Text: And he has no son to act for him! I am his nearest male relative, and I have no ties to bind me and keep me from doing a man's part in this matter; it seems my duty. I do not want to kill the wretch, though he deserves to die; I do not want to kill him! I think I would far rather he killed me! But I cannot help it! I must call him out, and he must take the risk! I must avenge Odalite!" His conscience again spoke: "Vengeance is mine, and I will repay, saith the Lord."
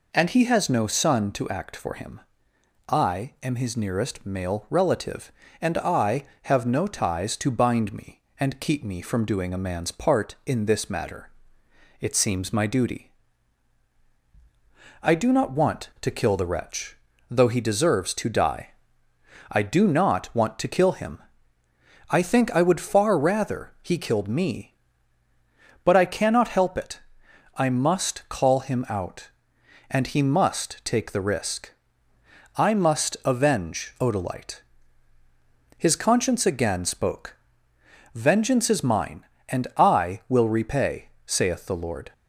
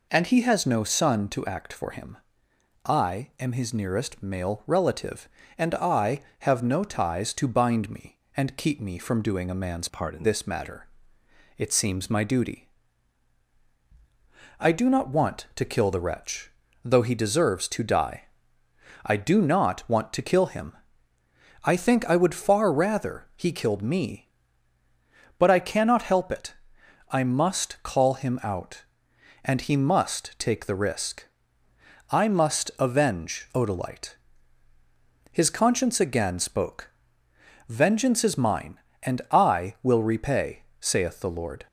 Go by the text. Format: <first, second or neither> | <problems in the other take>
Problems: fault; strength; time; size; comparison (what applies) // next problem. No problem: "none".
first | changes voice from "part" to "in"; from 9.8 to 10.2 s; 0.4 s long